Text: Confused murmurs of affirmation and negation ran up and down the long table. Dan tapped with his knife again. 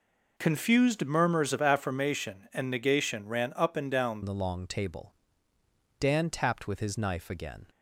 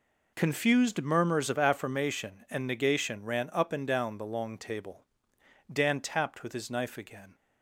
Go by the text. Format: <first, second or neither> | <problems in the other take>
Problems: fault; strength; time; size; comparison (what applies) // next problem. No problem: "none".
second | changes voice at "the"; from 4.2 s on; 3.4 s long